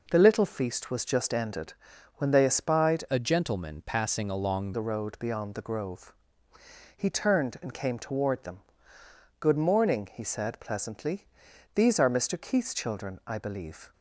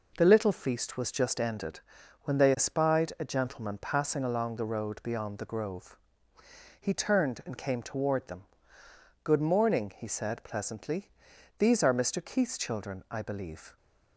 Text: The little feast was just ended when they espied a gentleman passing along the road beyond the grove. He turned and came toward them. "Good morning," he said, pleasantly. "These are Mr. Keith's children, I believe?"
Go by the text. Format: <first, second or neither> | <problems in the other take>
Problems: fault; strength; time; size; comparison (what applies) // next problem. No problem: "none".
second | pauses between "ended" and "when"; at 1.7 s; 0.42 s long; also in the second // changes voice from "a" to "along"; from 3.1 to 4.7 s; 1.6 s long